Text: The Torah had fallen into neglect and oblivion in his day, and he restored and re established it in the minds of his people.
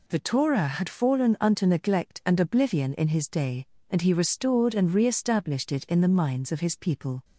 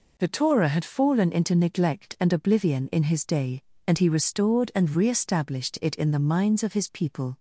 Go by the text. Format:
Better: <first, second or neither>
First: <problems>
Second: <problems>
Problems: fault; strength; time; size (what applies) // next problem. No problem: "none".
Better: second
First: says "unto" for "into"; at 1.4 s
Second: none